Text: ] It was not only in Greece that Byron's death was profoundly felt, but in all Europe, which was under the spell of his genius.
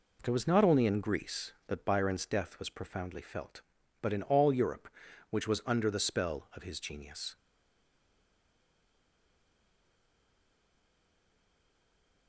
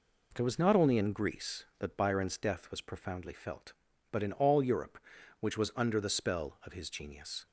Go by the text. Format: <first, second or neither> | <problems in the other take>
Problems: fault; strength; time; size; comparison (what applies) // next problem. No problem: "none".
second | stays silent after the last word; strong; from 7.3 s on; 4.9 s long